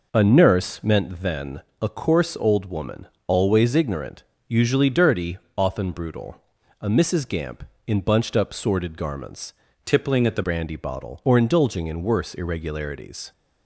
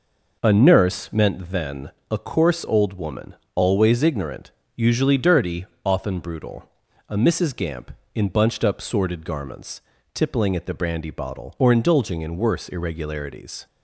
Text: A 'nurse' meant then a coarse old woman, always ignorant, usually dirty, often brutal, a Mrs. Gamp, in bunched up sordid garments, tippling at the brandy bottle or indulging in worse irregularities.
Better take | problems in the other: second | pauses between "then" and "a"; slight; at 1.6 s; 0.18 s long; slight in the second // changes voice from "tippling" to "the"; from 9.8 to 10.4 s; 0.6 s long

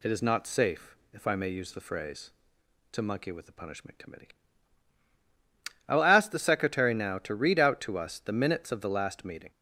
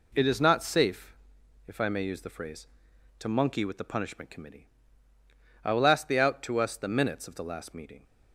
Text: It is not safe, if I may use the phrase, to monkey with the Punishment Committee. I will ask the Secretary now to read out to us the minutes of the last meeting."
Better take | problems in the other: first | skips "Secretary now to read"; at 6.1 s

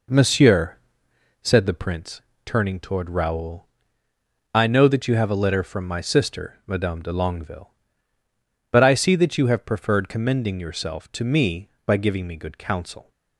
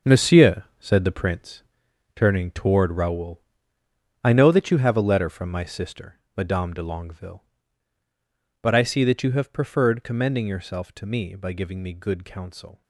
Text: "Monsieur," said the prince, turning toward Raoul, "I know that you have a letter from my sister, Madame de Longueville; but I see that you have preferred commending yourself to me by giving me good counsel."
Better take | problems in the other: first | gets quieter; strong; throughout; 10.5 dB

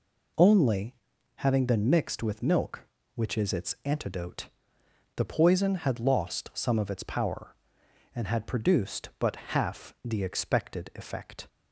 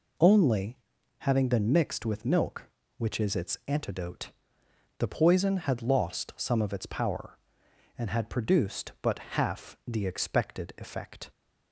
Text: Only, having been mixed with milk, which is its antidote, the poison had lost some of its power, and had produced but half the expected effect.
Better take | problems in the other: neither | none

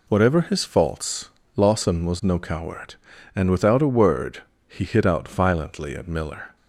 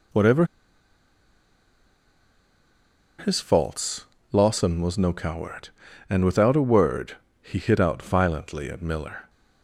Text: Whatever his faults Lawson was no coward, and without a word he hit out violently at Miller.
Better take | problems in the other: first | pauses between "Whatever" and "his"; strong; at 0.4 s; 2.7 s long // pauses between "faults" and "Lawson"; slight; at 4.0 s; 0.30 s long; slight in the first // pauses between "word" and "he"; slight; at 7.1 s; 0.26 s long; slight in the first

